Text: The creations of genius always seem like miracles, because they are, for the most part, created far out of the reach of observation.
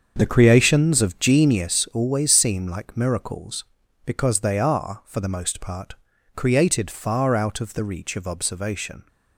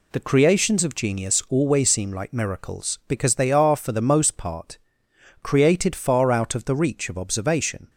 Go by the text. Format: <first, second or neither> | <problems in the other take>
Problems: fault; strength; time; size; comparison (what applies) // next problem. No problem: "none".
second | starts louder than the rest; until 1.4 s; 7 dB